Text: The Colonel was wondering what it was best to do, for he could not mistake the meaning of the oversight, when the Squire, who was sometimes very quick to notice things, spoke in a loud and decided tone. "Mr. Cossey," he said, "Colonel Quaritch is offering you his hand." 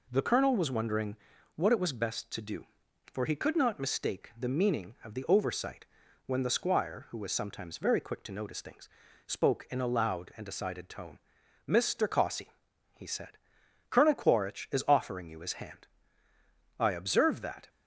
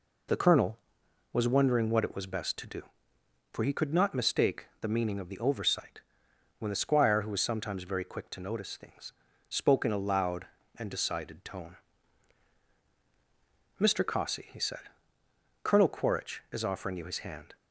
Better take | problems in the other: second | pauses between "wondering" and "what"; at 1.1 s; 0.38 s long // goes on to say "I observe that"; noticeable; from 16.7 s on; 0.90 s long

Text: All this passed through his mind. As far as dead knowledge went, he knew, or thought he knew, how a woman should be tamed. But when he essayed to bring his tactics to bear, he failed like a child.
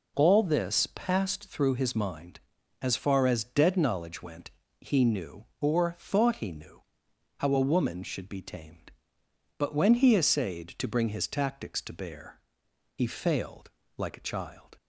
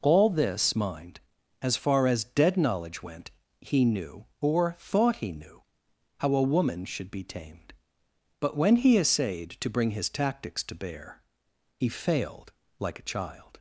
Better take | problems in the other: first | skips "passed through his"; at 0.7 s // pauses between "failed" and "like"; slight; at 12.5 s; 0.26 s long; slight in the first

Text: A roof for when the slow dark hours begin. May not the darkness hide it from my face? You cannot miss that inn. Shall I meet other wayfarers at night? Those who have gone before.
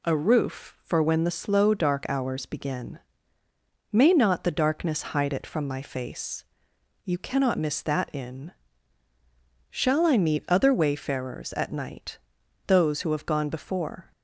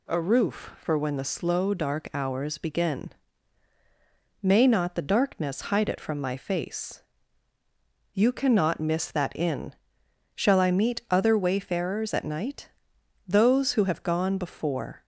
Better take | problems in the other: neither | none

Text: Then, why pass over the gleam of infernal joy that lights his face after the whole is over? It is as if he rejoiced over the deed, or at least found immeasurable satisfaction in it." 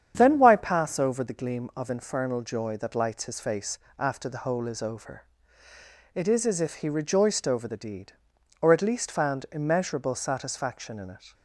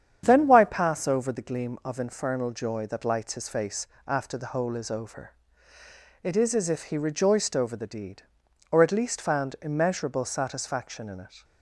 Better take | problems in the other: neither | starts louder than the rest; strong; the same in both // pauses between "face" and "after"; slight; the same in both

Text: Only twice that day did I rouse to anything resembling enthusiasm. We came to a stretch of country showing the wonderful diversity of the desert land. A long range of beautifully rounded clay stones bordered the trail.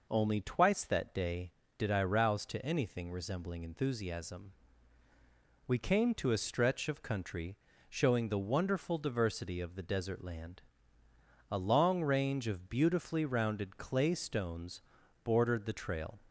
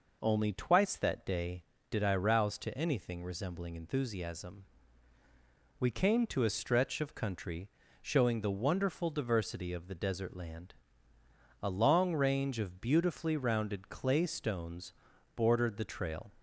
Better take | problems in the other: neither | pauses between "country" and "showing"; slight; the same in both // pauses between "stones" and "bordered"; the same in both

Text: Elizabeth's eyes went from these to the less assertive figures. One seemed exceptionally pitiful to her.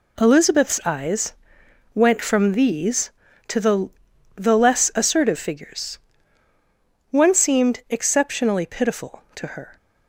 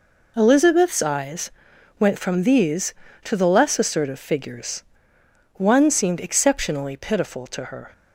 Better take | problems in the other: second | pauses between "eyes" and "went"; noticeable; at 1.3 s; 0.62 s long; noticeable in the second // says "the" twice; at 4.3 s

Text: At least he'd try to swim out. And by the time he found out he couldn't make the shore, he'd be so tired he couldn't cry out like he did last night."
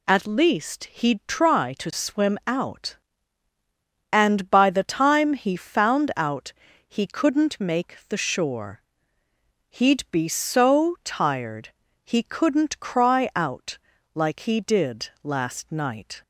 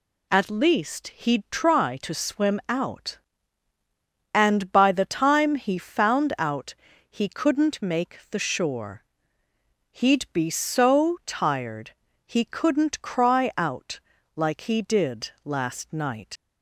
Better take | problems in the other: first | pauses between "out" and "he"; slight; at 6.7 s; 0.36 s long; slight in the first // pauses between "tired" and "he"; slight; at 11.9 s; 0.34 s long; slight in the first // pauses between "out" and "like"; slight; at 13.9 s; 0.35 s long; slight in the first // leaves "night" unfinished; at 16.3 s; 75 ms

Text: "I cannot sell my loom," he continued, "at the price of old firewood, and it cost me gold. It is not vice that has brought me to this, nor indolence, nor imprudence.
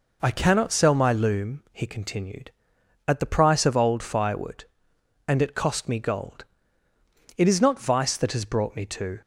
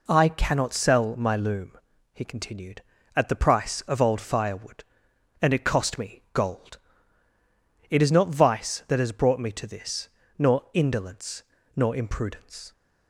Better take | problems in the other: second | stops before "this nor indolence nor imprudence"; at 9.2 s

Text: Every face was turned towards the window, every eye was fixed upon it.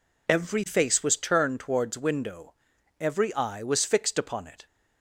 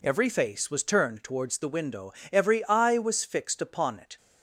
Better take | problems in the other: second | skips "the"; at 1.9 s

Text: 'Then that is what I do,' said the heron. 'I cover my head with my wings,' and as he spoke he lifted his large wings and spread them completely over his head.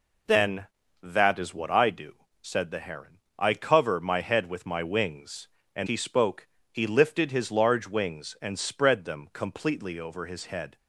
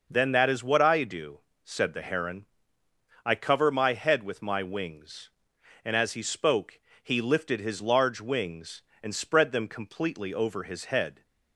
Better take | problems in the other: second | skips "as"; at 5.8 s // pauses between "spoke" and "he"; slight; at 6.4 s; 0.24 s long; slight in the second

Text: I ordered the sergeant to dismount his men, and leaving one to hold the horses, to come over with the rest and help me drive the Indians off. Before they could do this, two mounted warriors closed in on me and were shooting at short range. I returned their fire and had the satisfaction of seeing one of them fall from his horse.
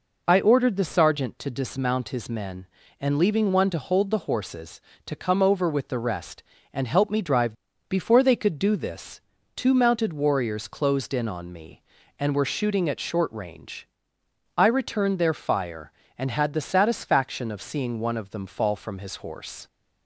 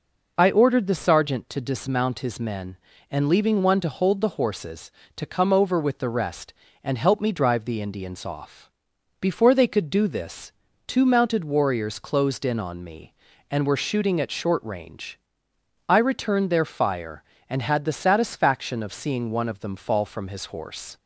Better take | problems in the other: second | skips "the Indians off"; at 7.7 s

